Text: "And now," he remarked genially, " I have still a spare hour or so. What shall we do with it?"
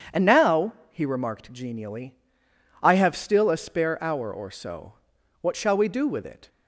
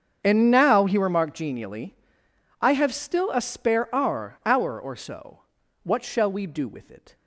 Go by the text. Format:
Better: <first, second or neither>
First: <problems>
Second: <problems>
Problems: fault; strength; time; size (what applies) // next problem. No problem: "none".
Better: first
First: starts louder than the rest; strong; until 1.3 s; 7.5 dB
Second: starts louder than the rest; until 1.2 s; 7 dB // says "hour" twice; at 4.4 s